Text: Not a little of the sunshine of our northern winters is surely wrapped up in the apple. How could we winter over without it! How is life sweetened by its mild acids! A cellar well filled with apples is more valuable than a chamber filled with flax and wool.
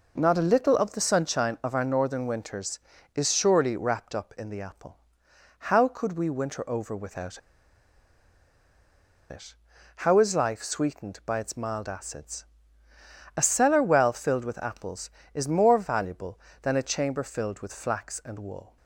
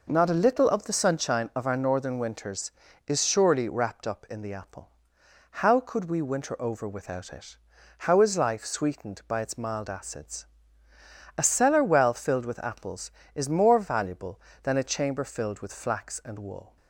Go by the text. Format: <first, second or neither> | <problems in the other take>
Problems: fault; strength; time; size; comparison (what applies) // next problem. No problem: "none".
second | pauses between "without" and "it"; strong; at 7.3 s; 1.9 s long